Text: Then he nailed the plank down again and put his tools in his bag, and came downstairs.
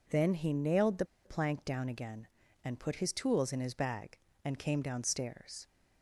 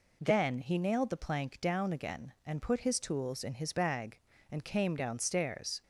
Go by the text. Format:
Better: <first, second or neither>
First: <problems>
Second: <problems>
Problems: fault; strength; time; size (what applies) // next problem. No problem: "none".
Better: second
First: pauses between "the" and "plank"; slight; at 1.0 s; 0.19 s long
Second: none